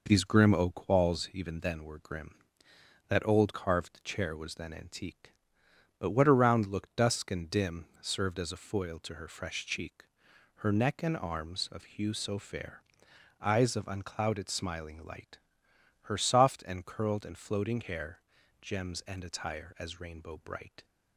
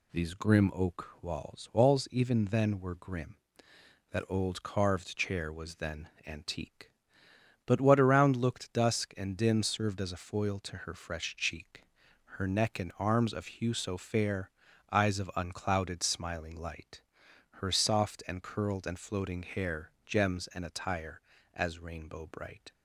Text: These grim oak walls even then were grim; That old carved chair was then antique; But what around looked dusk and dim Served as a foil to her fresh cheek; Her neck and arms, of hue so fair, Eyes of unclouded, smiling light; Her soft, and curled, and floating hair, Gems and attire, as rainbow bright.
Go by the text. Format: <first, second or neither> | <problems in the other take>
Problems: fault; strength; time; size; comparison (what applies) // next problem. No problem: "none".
first | says "walls" twice; at 1.7 s // pauses between "then" and "antique"; slight; at 6.0 s; 0.18 s long